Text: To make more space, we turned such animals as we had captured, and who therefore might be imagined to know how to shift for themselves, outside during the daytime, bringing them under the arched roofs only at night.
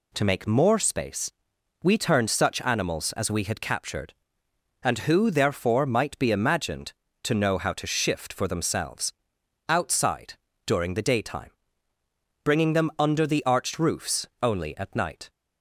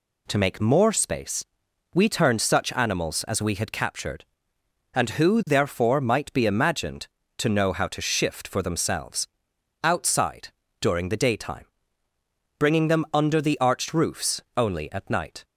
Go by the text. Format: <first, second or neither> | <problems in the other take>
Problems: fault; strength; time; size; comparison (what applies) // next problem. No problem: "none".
neither | pauses between "outside" and "during"; slight; the same in both // pauses between "roofs" and "only"; slight; the same in both